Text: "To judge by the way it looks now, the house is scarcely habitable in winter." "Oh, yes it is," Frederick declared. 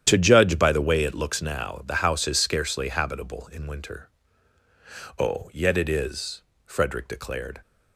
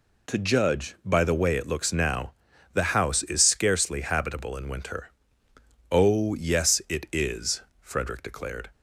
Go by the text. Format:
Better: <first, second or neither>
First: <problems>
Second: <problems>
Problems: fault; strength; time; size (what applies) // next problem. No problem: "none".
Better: second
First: starts louder than the rest; strong; until 1.0 s; 10 dB // says "yet" for "yes"; at 5.5 s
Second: none